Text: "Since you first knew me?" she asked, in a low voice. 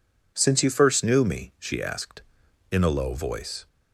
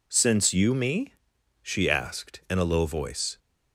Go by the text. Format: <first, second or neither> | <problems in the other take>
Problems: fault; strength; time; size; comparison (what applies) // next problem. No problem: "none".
first | skips "first knew"; at 0.7 s